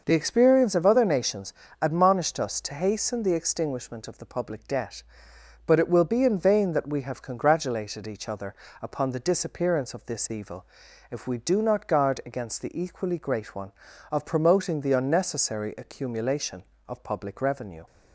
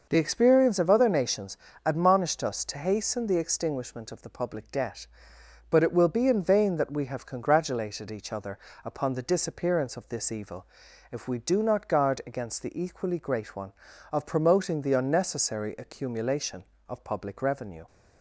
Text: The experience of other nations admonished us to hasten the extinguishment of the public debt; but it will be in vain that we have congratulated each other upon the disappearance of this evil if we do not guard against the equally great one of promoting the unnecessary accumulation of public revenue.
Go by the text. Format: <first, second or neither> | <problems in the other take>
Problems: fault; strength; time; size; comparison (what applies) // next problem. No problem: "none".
neither | pauses between "nations" and "admonished"; slight; the same in both // pauses between "other" and "upon"; slight; the same in both // pauses between "evil" and "if"; the same in both